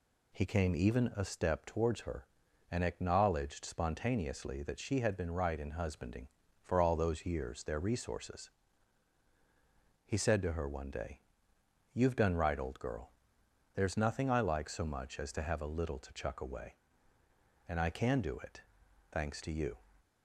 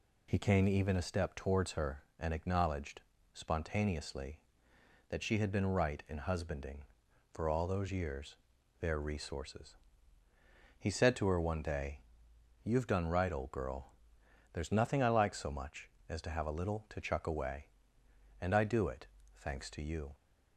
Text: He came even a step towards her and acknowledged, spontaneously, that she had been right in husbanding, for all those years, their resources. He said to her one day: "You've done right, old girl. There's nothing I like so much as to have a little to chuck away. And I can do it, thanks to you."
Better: first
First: none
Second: skips "can"; at 18.6 s

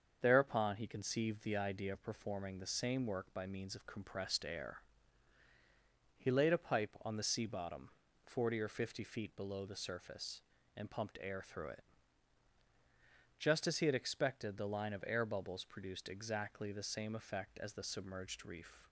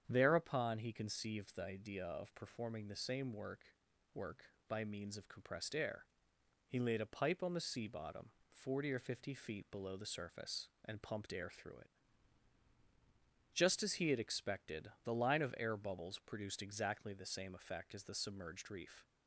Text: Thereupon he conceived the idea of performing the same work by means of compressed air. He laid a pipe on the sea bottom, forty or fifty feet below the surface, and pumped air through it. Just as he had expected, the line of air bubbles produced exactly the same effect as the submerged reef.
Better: first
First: starts louder than the rest; until 1.2 s; 7 dB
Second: starts louder than the rest; strong; until 1.0 s; 8 dB // says "work" twice; at 4.1 s

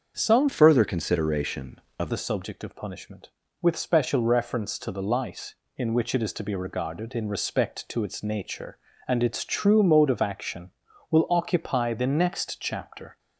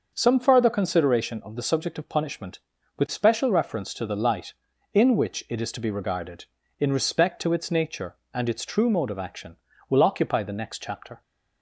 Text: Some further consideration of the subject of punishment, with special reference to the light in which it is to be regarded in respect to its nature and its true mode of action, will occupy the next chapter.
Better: second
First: starts louder than the rest; until 1.1 s; 7 dB // changes voice from "further" to "of"; from 0.4 to 2.1 s; 1.7 s long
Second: starts louder than the rest; until 1.1 s; 6.5 dB

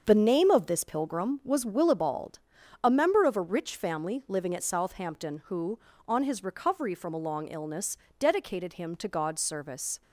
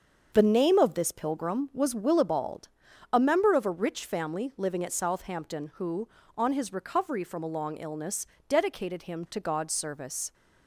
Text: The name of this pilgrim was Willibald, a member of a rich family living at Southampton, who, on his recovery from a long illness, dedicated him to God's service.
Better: neither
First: starts louder than the rest; until 1.0 s; 7 dB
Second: starts louder than the rest; until 1.3 s; 7 dB

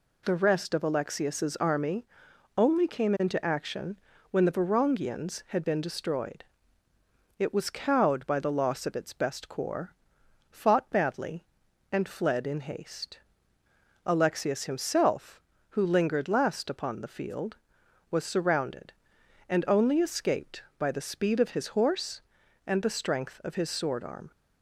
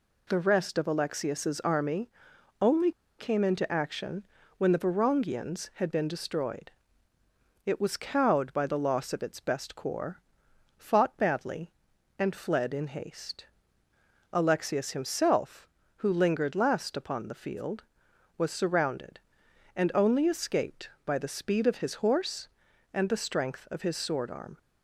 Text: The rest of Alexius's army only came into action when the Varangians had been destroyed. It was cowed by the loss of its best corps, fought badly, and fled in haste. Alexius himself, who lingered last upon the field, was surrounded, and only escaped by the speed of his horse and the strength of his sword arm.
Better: first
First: pauses between "army" and "only"; noticeable; at 2.0 s; 0.50 s long // pauses between "action" and "when"; slight; at 3.9 s; 0.36 s long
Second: pauses between "army" and "only"; noticeable; at 2.1 s; 0.50 s long // pauses between "only" and "came"; slight; at 2.9 s; 0.28 s long // pauses between "action" and "when"; slight; at 4.2 s; 0.36 s long

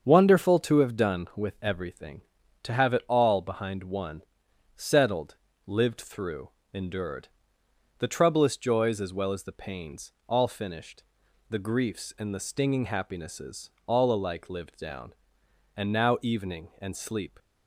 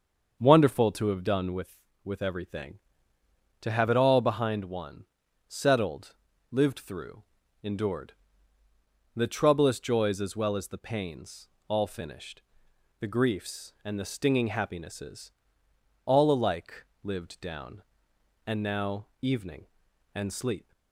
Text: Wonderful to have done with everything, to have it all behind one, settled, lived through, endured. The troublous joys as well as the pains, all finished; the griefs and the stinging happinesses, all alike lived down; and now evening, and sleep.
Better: first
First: starts louder than the rest; until 1.0 s; 7 dB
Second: starts louder than the rest; until 1.4 s; 6.5 dB // says "with" twice; at 2.0 s // pauses between "alike" and "lived"; slight; at 16.8 s; 0.16 s long // pauses between "now" and "evening"; slight; at 19.0 s; 0.16 s long

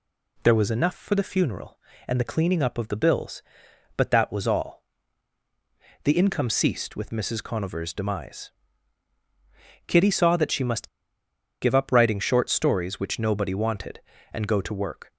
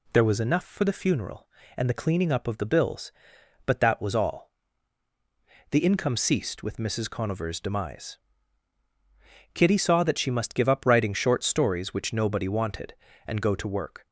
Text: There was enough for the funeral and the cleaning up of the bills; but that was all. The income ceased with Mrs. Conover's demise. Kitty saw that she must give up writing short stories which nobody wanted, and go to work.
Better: second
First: pauses between "must" and "give"; noticeable; at 10.8 s; 0.74 s long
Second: none

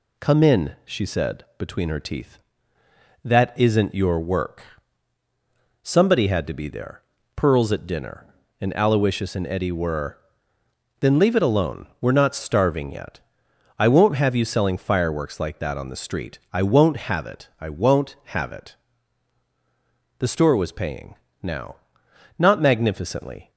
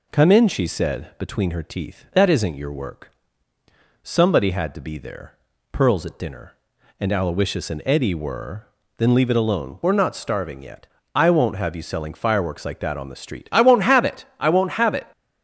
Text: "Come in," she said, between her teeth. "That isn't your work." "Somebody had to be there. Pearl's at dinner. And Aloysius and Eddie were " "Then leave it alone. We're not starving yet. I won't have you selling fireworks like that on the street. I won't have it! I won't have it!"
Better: second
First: goes on to say "The store was paying now Not magnificently"; strong; from 20.1 s on; 3.3 s long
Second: none

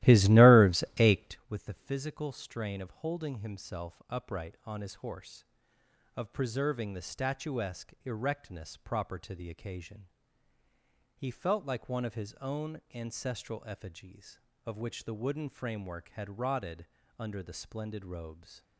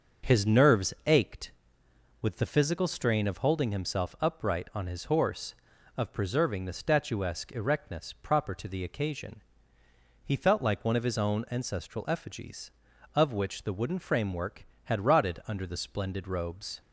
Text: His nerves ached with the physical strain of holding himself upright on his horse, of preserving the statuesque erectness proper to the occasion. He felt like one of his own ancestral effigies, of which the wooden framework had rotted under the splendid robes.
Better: second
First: starts louder than the rest; strong; until 1.4 s; 15.5 dB // pauses between "rotted" and "under"; slight; at 16.8 s; 0.32 s long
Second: none

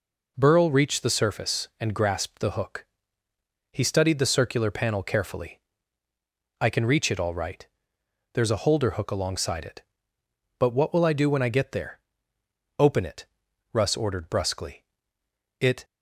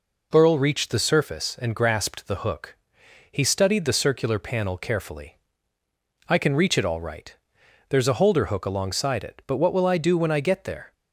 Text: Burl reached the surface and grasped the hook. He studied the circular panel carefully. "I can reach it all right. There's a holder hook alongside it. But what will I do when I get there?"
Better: second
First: goes on to say "Open it Russ ordered brusquely It"; strong; from 12.8 s on; 3.0 s long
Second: none

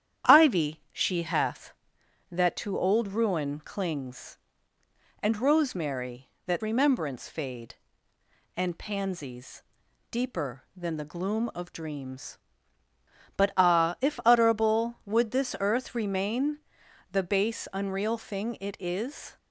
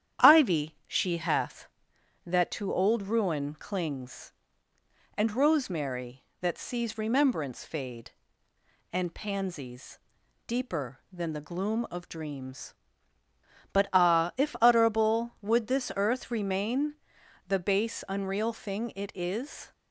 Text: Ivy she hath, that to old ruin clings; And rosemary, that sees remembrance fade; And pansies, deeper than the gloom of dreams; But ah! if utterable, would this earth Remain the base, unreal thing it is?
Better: second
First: starts louder than the rest; strong; until 1.3 s; 10 dB // skips "sees"; at 6.6 s // pauses between "Remain" and "the"; noticeable; at 16.6 s; 0.52 s long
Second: starts louder than the rest; strong; until 1.3 s; 10 dB // pauses between "Remain" and "the"; noticeable; at 16.9 s; 0.52 s long

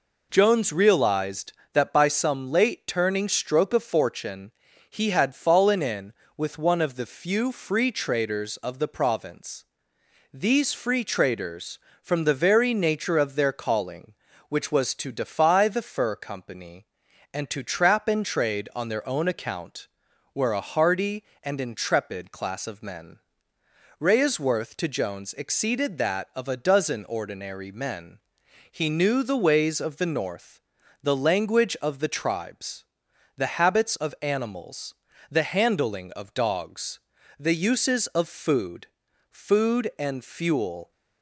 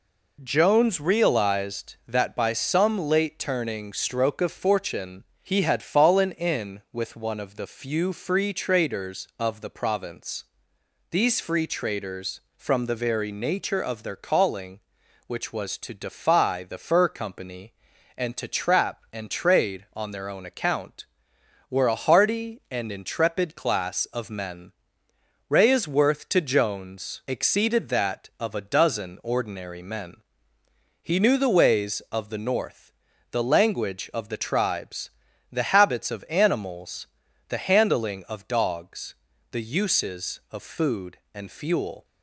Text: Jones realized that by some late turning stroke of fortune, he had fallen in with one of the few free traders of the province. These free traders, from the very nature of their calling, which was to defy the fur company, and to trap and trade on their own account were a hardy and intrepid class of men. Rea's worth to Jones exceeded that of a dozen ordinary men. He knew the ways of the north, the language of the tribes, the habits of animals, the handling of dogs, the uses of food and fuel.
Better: second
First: says "food" twice; at 39.3 s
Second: none

